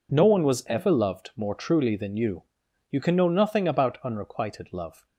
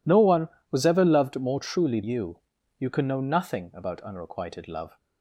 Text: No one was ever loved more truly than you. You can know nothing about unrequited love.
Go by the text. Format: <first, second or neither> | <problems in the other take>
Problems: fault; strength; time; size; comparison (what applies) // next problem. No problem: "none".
first | skips "than"; at 2.0 s